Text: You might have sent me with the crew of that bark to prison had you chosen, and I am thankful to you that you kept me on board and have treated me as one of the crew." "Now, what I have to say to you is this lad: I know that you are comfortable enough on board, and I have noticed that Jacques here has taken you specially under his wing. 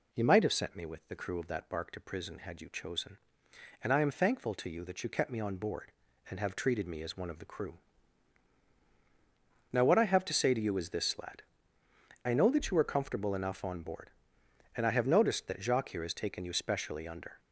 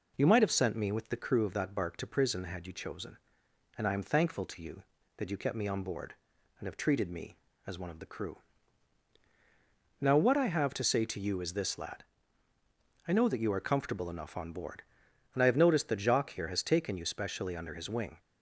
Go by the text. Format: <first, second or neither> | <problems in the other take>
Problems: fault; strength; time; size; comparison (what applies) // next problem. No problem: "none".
second | stops before "his wing"; at 17.3 s